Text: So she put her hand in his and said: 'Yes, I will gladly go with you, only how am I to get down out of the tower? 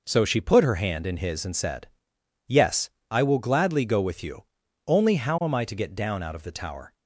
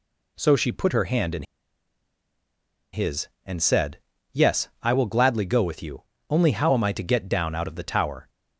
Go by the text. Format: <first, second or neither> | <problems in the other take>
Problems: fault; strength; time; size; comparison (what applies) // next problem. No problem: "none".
first | pauses between "in" and "his"; strong; at 1.4 s; 1.4 s long